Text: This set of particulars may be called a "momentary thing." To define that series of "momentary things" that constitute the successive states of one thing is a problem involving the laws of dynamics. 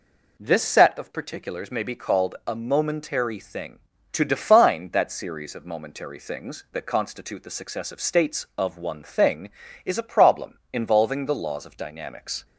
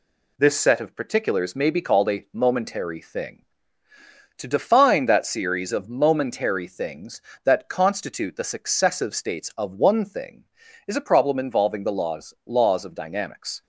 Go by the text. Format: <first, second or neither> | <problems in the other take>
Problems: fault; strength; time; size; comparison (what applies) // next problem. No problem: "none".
first | says "laws" twice; at 12.4 s